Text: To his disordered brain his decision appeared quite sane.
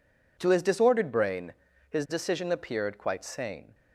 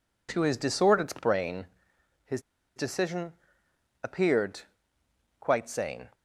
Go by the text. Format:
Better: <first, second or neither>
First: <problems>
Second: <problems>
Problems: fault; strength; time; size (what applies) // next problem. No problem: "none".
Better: first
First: pauses between "brain" and "his"; slight; at 1.5 s; 0.36 s long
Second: pauses between "brain" and "his"; noticeable; at 1.6 s; 0.58 s long // pauses between "his" and "decision"; at 2.3 s; 0.36 s long // pauses between "decision" and "appeared"; noticeable; at 3.3 s; 0.68 s long // pauses between "appeared" and "quite"; noticeable; at 4.6 s; 0.80 s long